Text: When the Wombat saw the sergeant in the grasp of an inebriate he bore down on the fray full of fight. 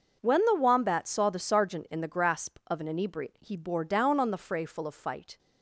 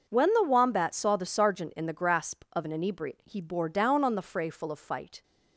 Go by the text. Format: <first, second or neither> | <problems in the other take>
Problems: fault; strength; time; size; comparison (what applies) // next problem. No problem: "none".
neither | none